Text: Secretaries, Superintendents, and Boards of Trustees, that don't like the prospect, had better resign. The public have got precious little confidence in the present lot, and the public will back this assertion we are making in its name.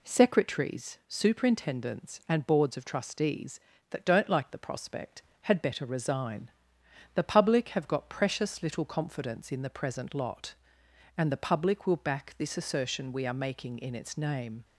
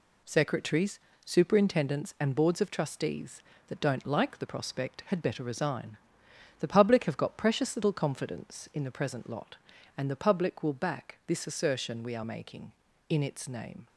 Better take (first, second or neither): neither